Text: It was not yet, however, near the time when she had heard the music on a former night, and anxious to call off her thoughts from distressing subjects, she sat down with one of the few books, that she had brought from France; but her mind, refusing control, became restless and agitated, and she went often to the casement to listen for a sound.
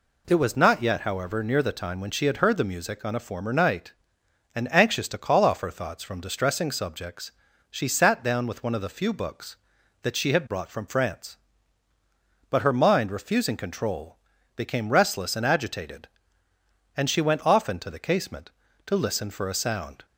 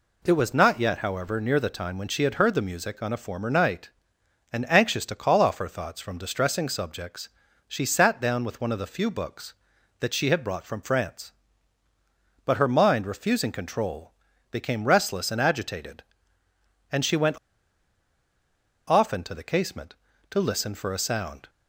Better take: first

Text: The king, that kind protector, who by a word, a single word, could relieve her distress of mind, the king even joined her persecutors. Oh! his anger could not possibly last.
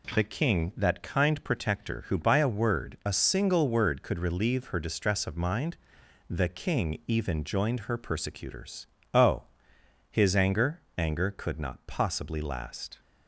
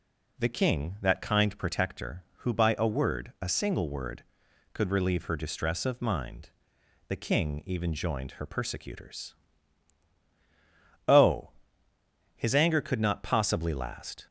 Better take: second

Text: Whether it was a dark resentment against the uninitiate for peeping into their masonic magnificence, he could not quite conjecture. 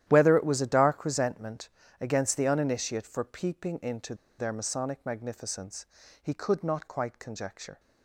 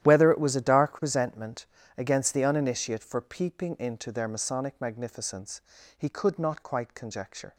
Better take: second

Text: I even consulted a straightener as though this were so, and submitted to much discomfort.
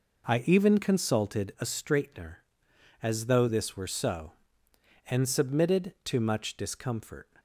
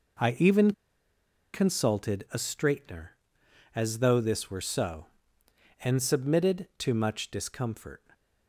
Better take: first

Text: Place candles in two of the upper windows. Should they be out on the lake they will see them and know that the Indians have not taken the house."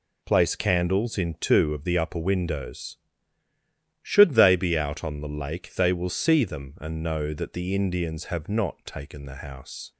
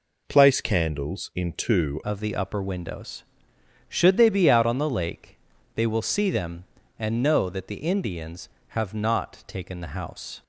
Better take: first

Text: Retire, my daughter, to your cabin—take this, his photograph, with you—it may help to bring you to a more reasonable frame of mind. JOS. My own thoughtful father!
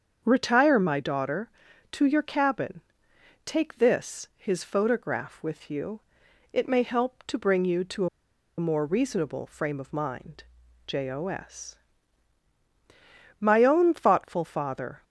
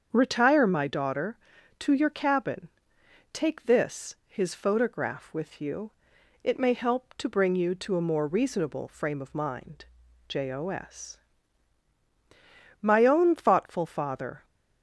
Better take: second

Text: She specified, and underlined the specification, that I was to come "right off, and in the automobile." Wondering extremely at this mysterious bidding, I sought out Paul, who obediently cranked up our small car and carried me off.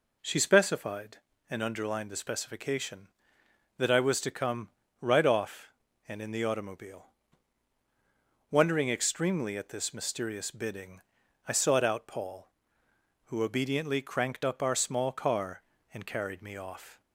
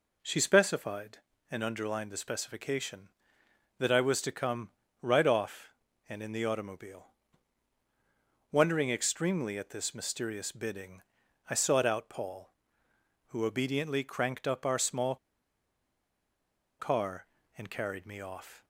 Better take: first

